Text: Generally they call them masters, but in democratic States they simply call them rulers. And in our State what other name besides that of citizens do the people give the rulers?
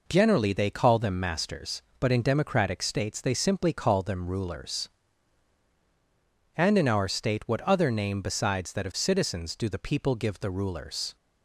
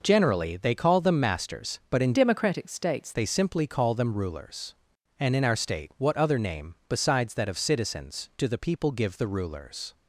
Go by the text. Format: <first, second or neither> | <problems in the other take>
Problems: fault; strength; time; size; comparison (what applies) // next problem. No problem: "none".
first | changes voice from "democratic" to "States"; from 2.1 to 3.1 s; 1.0 s long